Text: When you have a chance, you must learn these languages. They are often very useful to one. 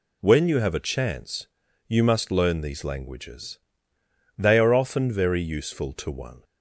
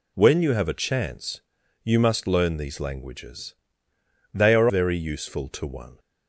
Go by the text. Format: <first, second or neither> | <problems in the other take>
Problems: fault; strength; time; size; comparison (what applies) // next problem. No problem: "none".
first | skips "often"; at 4.6 s